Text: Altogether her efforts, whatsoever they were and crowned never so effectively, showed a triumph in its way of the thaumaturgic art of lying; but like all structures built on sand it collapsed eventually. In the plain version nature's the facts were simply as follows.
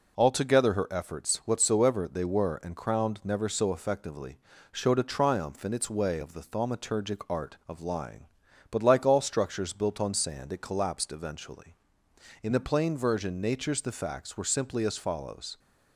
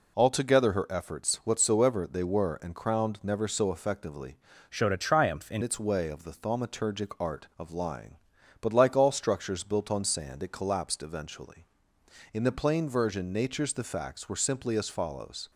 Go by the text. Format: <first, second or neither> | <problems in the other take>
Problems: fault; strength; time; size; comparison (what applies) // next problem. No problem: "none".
first | changes voice from "showed" to "in"; from 4.7 to 5.6 s; 0.9 s long